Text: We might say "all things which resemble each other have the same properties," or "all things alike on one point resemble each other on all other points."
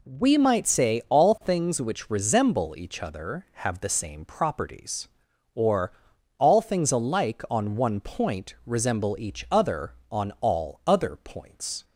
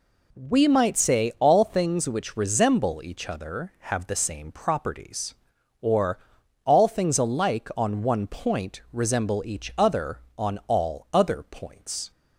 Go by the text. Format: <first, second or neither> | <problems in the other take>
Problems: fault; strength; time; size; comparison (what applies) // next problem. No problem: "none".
neither | pauses between "or" and "all"; noticeable; the same in both